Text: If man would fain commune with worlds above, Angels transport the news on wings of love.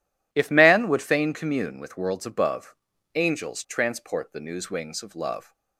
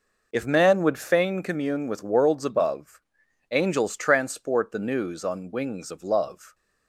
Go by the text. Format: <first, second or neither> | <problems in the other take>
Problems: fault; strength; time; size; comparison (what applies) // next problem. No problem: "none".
second | skips "on"; at 4.6 s